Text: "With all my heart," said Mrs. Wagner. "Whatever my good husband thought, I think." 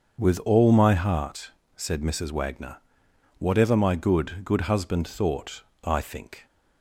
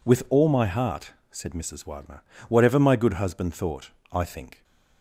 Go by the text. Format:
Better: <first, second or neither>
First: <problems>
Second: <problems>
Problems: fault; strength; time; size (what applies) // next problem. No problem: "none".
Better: second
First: starts louder than the rest; until 1.2 s; 6.5 dB // says "good" twice; at 4.4 s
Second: none